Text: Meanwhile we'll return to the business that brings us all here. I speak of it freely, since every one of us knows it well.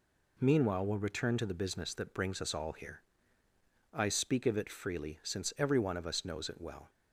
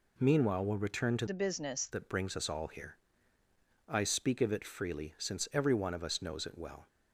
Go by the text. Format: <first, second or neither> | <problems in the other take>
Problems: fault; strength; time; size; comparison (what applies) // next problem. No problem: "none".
first | changes voice from "the" to "business"; from 1.2 to 1.8 s; 0.6 s long